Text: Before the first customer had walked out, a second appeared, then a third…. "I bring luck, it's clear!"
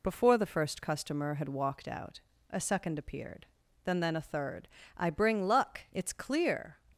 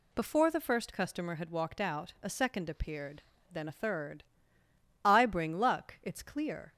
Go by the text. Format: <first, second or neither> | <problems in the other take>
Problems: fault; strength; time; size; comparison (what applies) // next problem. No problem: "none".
second | says "then" twice; at 3.9 s